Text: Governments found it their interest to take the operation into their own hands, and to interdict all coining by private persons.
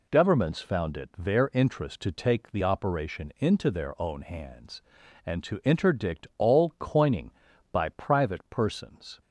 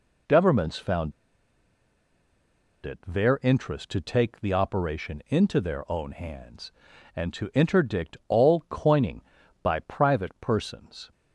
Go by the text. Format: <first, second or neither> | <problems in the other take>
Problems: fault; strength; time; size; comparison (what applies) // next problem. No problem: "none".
first | pauses between "found" and "it"; strong; at 1.1 s; 1.7 s long